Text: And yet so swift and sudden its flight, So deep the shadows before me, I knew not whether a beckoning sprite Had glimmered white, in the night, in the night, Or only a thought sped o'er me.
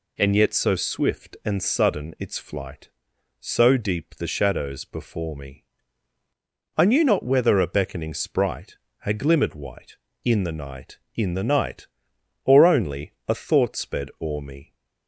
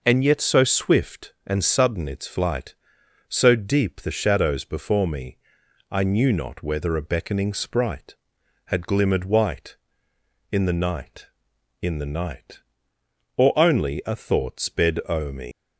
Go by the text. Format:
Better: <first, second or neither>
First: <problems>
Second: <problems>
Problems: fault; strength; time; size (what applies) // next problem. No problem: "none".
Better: first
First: none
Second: leaves "me" unfinished; at 15.5 s; 160 ms